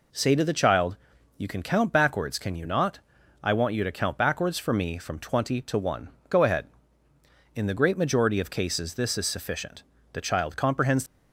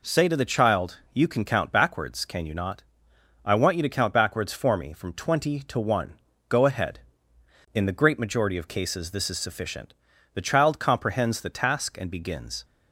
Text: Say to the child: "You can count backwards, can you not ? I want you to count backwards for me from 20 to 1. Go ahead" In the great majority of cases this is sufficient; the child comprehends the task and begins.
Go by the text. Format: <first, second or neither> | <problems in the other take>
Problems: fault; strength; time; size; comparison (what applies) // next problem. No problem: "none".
second | stops before "the task and begins"; at 11.0 s